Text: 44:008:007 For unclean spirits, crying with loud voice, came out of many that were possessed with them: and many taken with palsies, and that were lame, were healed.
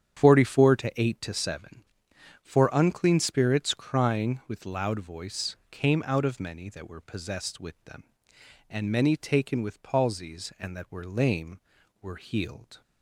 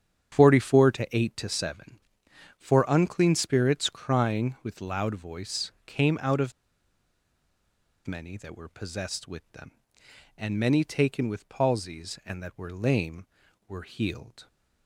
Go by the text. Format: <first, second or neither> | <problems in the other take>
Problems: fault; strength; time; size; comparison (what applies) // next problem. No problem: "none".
first | starts louder than the rest; strong; until 1.4 s; 9 dB; strong in the first // pauses between "of" and "many"; strong; at 6.5 s; 1.5 s long